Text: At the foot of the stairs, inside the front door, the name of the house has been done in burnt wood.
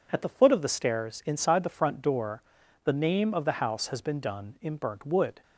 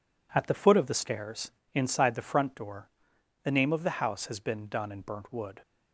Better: first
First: none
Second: gets quieter; strong; throughout; 9 dB

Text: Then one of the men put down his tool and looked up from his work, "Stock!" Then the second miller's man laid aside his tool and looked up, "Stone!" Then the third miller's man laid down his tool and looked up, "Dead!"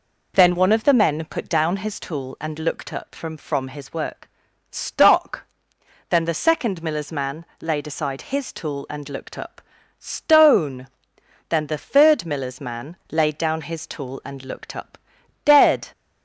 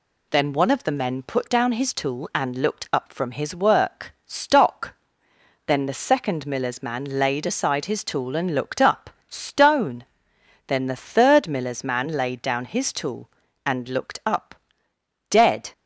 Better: second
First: says "from" twice; at 3.3 s // pauses between "man" and "laid"; slight; at 7.4 s; 0.16 s long // pauses between "man" and "laid"; slight; at 12.9 s; 0.16 s long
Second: none

